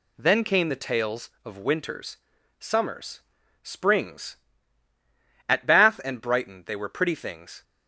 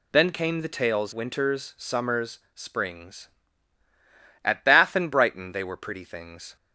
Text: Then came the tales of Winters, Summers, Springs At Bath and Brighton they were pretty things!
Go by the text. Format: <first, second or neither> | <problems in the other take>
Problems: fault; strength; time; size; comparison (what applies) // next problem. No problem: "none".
first | skips "of"; at 1.1 s